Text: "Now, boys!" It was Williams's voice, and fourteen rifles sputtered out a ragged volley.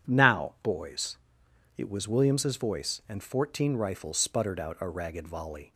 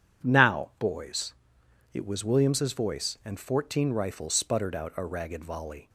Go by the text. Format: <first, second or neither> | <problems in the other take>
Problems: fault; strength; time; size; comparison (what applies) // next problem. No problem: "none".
neither | none